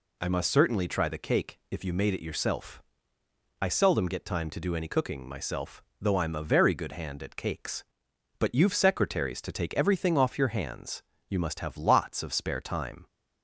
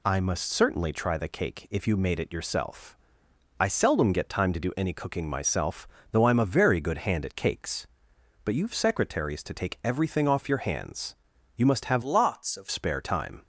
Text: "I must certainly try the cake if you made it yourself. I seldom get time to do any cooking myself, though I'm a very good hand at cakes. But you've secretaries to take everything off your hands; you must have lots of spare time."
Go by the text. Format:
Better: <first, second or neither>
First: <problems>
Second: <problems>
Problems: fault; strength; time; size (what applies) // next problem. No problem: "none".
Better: first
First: none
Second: changes voice from "lots" to "of"; from 12.0 to 12.6 s; 0.6 s long